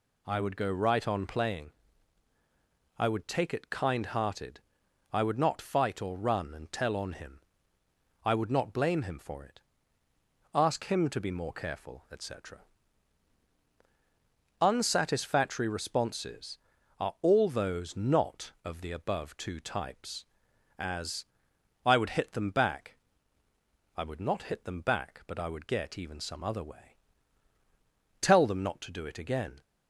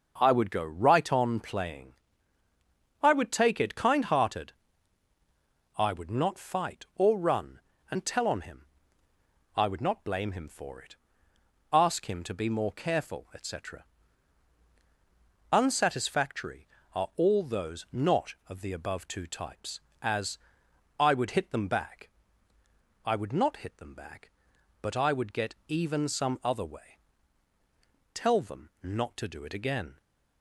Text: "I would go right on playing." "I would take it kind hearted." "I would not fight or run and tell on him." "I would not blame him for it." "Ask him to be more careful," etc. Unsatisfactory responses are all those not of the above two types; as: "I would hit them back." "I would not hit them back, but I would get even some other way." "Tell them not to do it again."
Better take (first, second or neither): first